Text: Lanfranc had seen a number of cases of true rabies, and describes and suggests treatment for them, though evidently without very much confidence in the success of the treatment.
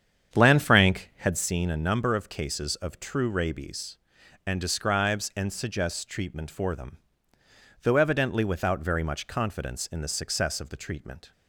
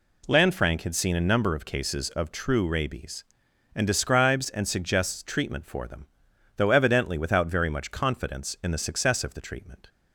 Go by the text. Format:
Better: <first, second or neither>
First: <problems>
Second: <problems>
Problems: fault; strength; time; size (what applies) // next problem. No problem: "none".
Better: second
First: starts louder than the rest; strong; until 1.5 s; 8.5 dB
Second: none